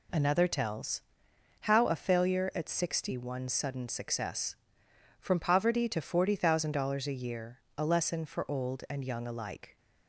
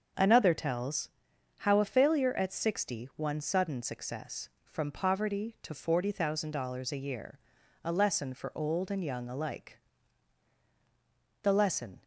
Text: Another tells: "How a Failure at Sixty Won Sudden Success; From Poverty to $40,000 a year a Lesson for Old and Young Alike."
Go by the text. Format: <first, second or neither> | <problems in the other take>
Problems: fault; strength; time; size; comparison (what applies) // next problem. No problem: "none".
first | starts louder than the rest; until 1.6 s; 6.5 dB // pauses between "year" and "a"; at 7.4 s; 0.42 s long; slight in the first // goes on to say "The lesson"; noticeable; from 11.4 s on; 0.62 s long